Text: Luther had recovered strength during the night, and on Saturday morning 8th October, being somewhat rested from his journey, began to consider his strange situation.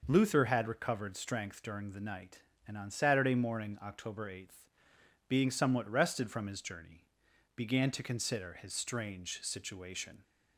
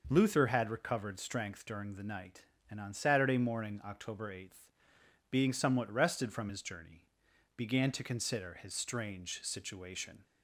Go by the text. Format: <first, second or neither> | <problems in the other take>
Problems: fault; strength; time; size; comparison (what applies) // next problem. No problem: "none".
neither | none